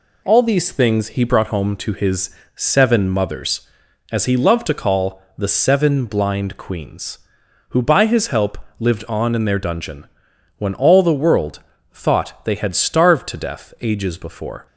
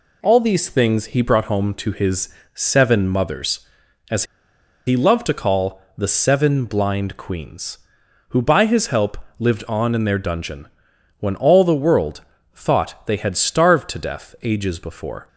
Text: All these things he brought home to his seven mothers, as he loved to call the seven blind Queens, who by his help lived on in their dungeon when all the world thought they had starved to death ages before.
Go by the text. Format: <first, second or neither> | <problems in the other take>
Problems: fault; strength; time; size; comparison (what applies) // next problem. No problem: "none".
first | pauses between "his" and "seven"; slight; at 2.2 s; 0.24 s long; slight in the first // pauses between "as" and "he"; noticeable; at 4.2 s; 0.62 s long // pauses between "call" and "the"; slight; at 5.7 s; 0.16 s long; slight in the first // pauses between "help" and "lived"; slight; at 9.1 s; 0.20 s long; slight in the first // pauses between "dungeon" and "when"; noticeable; at 10.6 s; 0.52 s long; noticeable in the first // pauses between "world" and "thought"; slight; at 12.2 s; 0.34 s long; slight in the first